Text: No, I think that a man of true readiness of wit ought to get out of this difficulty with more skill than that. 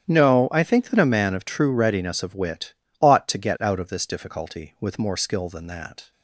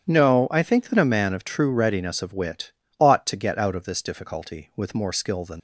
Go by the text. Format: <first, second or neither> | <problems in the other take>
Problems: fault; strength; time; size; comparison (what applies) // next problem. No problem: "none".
first | starts louder than the rest; strong; until 1.0 s; 9.5 dB; strong in the first // pauses between "wit" and "ought"; slight; at 2.7 s; 0.26 s long; slight in the first // stops before "that"; at 5.5 s